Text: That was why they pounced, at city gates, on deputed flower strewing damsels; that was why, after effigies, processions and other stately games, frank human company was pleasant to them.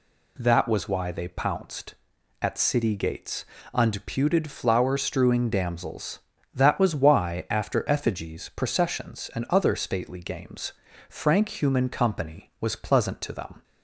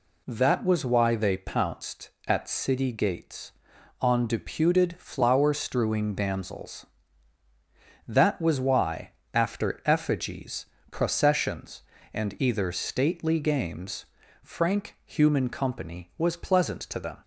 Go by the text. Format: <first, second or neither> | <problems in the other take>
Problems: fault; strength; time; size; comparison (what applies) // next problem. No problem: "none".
first | says "either" for "other"; at 12.3 s